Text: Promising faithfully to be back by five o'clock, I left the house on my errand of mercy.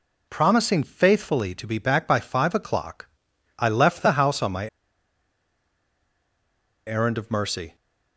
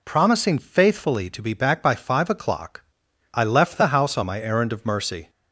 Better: second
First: pauses between "my" and "errand"; strong; at 4.6 s; 2.1 s long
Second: none

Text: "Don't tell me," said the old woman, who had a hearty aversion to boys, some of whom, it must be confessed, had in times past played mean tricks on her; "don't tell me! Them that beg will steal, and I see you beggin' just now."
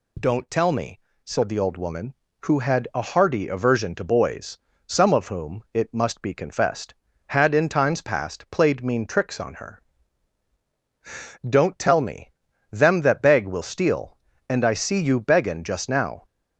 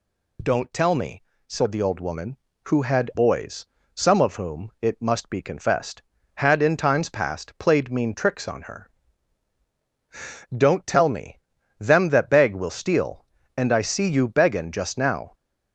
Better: first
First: none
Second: skips "a hearty aversion to"; at 3.1 s

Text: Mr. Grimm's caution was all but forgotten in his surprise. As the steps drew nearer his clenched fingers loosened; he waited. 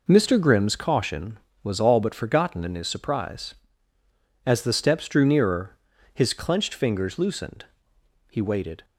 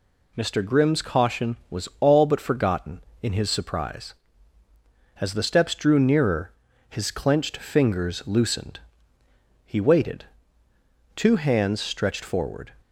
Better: first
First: pauses between "nearer" and "his"; at 5.7 s; 0.42 s long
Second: pauses between "nearer" and "his"; at 6.5 s; 0.38 s long // goes on to say "Two hands stretched forward"; from 11.1 s on; 1.5 s long

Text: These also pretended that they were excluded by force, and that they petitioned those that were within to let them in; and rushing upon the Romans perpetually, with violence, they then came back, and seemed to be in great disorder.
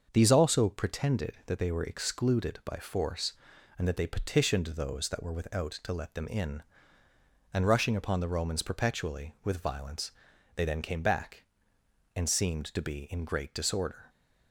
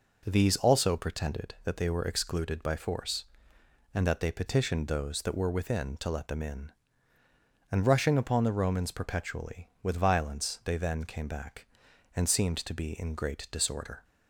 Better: second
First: starts louder than the rest; until 1.1 s; 6.5 dB // says "without" for "within"; at 5.3 s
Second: none

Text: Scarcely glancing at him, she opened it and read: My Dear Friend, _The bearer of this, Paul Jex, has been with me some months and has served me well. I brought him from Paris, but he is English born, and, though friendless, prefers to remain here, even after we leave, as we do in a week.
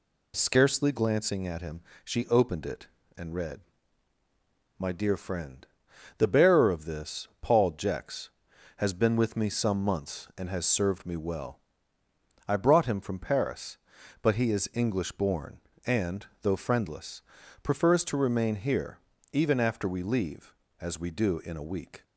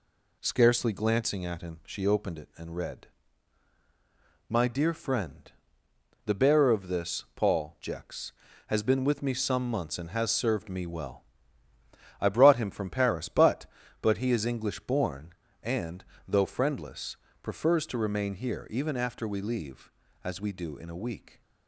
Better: first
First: none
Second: says "but" twice; at 14.0 s

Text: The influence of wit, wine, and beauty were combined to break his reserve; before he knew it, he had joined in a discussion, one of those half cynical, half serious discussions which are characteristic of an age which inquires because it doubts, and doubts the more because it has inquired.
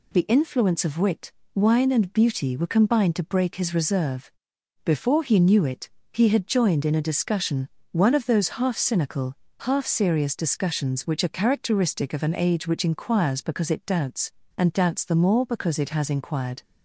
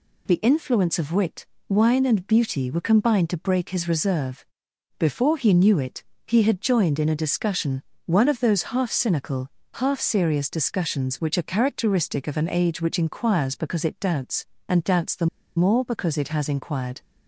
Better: first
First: none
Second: pauses between "the" and "more"; slight; at 15.2 s; 0.29 s long

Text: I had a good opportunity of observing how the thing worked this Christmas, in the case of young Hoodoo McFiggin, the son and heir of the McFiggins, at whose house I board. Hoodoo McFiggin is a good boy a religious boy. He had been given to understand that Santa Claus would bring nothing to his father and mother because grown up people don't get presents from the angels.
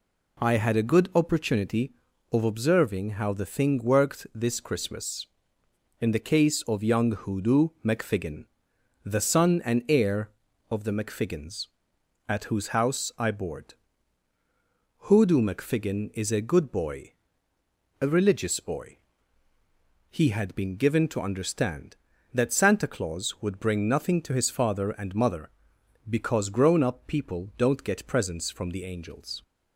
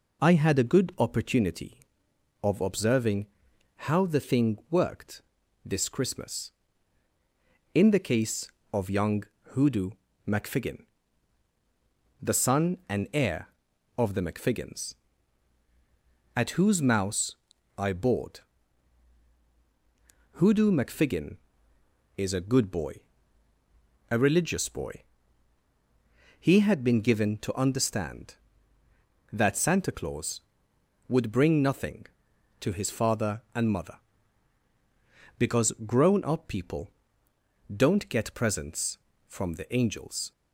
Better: first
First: pauses between "boy" and "a"; noticeable; at 17.1 s; 0.88 s long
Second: pauses between "observing" and "how"; noticeable; at 3.2 s; 0.60 s long // pauses between "worked" and "this"; at 5.2 s; 0.42 s long // pauses between "young" and "Hoodoo"; slight; at 9.2 s; 0.28 s long // pauses between "Hoodoo" and "McFiggin"; slight; at 9.9 s; 0.36 s long // says "mouse" for "house"; at 16.8 s // pauses between "boy" and "a"; at 22.9 s; 1.1 s long // pauses between "people" and "don't"; noticeable; at 36.8 s; 0.82 s long

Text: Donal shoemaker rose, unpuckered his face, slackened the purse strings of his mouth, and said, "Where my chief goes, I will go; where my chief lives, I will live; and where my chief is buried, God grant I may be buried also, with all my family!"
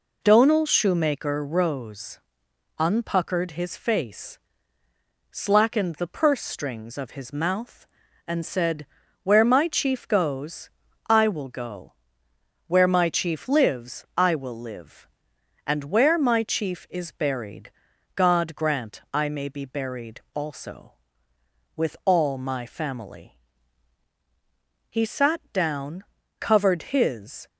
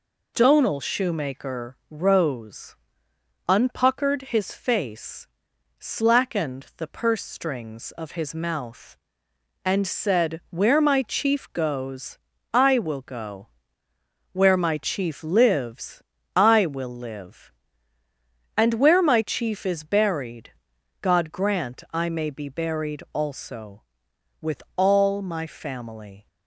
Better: second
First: goes on to say "He sat down covered his"; strong; from 24.8 s on; 2.6 s long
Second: none

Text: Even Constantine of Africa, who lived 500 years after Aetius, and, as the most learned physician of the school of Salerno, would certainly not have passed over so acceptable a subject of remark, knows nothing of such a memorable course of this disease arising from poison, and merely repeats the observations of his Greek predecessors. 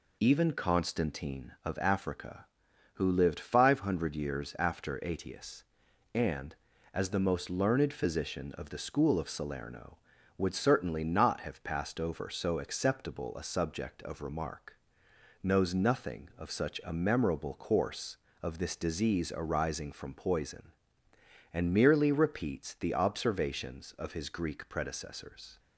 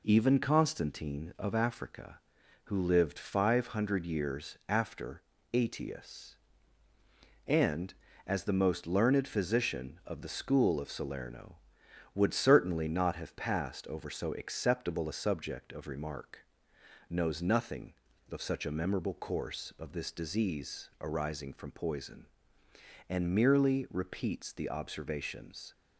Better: first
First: none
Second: pauses between "after" and "Aetius"; slight; at 5.2 s; 0.28 s long // stops before "of his Greek predecessors"; at 25.7 s

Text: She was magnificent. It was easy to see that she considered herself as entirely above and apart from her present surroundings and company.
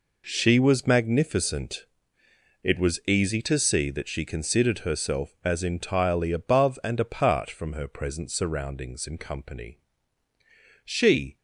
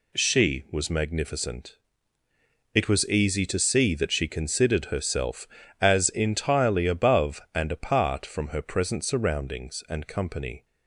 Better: second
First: goes on to say "She"; from 10.8 s on; 0.54 s long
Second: none

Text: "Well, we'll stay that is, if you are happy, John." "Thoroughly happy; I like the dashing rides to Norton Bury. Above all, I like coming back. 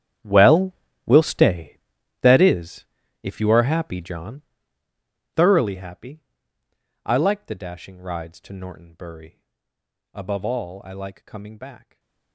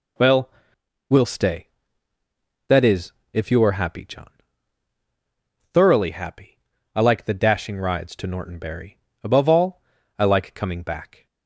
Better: second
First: gets quieter; strong; throughout; 18 dB // stays silent after the last word; slight; from 11.7 s on; 0.6 s long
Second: none

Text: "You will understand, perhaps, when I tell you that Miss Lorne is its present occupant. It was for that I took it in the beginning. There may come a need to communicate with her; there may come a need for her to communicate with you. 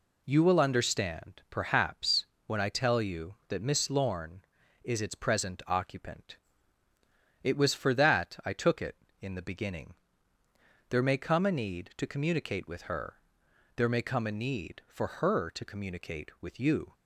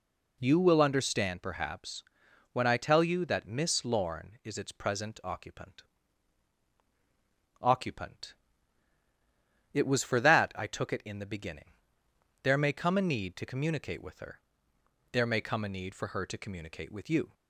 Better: first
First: none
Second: says "occupant" twice; at 7.6 s

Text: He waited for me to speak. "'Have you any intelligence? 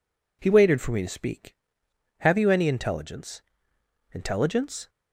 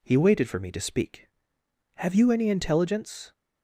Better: second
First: says "intelligence" twice; at 4.1 s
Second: none

